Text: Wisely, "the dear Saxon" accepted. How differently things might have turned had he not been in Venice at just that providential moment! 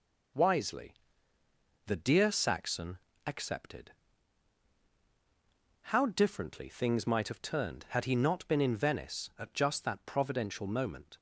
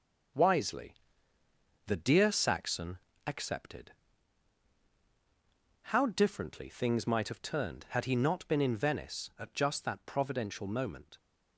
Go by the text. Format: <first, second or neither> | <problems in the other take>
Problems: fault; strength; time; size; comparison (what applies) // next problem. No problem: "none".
first | gets quieter; noticeable; throughout; 5.5 dB // pauses between "Saxon" and "accepted"; slight; at 2.9 s; 0.26 s long; slight in the first